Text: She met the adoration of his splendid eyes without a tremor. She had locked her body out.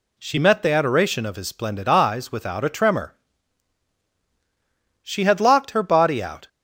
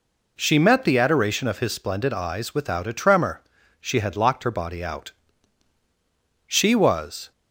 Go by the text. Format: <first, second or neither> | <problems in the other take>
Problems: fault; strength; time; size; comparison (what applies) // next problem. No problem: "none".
first | goes on to say "She was"; noticeable; from 6.4 s on; 0.86 s long